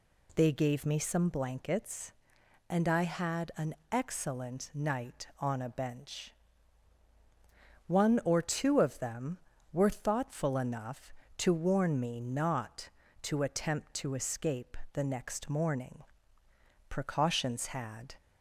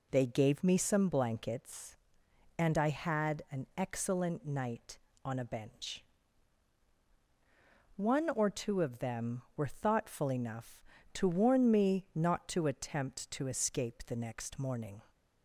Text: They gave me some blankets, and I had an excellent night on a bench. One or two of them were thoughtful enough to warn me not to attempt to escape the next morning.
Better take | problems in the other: second | pauses between "an" and "excellent"; slight; at 3.7 s; 0.16 s long // pauses between "escape" and "the"; slight; at 14.7 s; 0.16 s long // goes on to say "Precautions had"; noticeable; from 16.8 s on; 1.2 s long

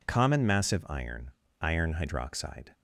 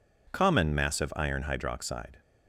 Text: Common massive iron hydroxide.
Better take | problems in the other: second | says "iron" twice; at 1.6 s

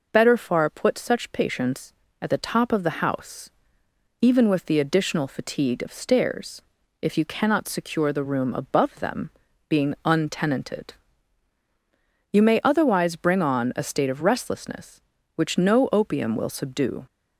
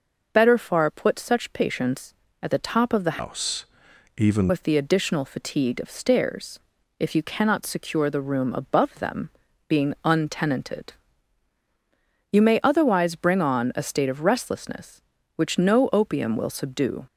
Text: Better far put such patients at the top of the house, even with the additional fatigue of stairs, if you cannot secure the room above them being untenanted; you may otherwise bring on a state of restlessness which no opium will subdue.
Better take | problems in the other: first | changes voice from "house" to "even"; from 3.1 to 4.5 s; 1.4 s long // pauses between "them" and "being"; at 9.2 s; 0.38 s long; also in the first

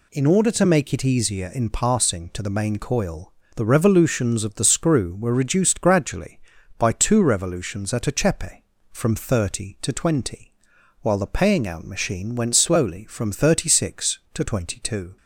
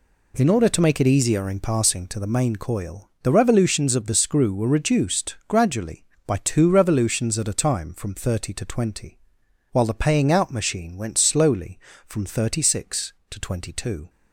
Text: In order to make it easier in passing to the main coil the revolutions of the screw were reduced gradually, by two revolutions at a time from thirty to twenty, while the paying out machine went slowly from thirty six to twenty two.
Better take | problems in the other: second | pauses between "coil" and "the"; slight; at 3.3 s; 0.24 s long // says "chepe" for "time"; at 8.1 s

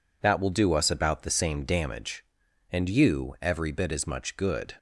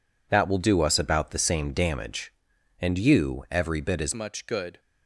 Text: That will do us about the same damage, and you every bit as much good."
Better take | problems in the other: first | changes voice at "much"; from 4.1 s on; 0.6 s long

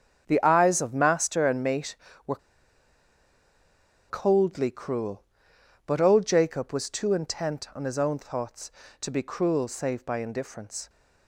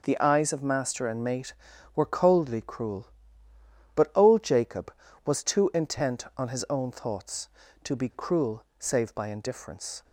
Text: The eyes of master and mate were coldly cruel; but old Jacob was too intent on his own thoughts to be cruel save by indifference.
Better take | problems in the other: second | starts louder than the rest; strong; until 1.2 s; 7.5 dB // pauses between "were" and "coldly"; strong; at 2.3 s; 1.7 s long

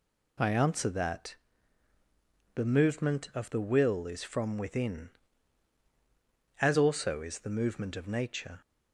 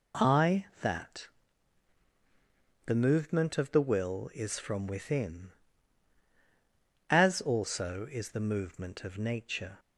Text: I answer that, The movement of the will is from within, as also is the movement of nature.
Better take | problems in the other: first | skips "answer"; at 0.7 s

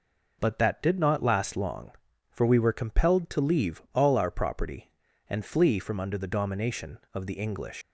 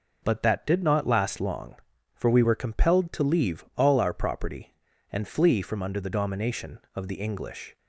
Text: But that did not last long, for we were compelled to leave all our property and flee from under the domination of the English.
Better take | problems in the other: second | leaves "English" unfinished; at 7.8 s; 145 ms

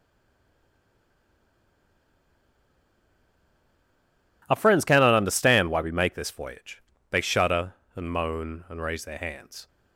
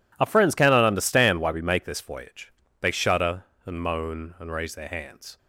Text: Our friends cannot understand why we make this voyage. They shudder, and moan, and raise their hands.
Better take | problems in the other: second | stays silent before the first word; strong; until 4.4 s; 4.4 s long

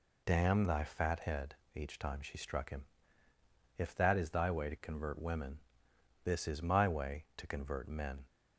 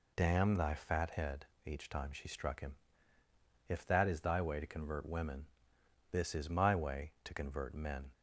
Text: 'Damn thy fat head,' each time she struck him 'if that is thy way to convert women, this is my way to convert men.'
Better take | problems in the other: neither | pauses between "him" and "if"; noticeable; the same in both

